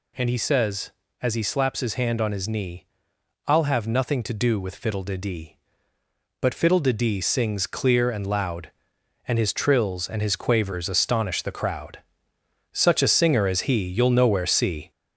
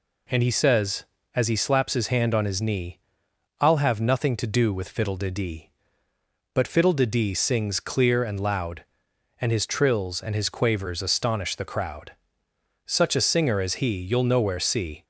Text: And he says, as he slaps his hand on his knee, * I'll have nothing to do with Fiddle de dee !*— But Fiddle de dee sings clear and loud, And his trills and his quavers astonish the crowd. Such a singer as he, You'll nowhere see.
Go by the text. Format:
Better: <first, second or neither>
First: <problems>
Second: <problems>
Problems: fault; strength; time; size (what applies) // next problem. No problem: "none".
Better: second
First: gets louder; noticeable; throughout; 4.5 dB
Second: none